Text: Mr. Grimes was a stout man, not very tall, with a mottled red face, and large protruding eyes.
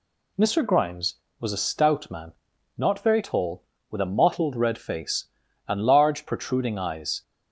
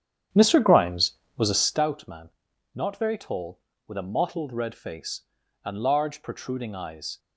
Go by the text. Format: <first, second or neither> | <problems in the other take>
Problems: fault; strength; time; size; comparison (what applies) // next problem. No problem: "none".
first | starts louder than the rest; strong; until 1.8 s; 9.5 dB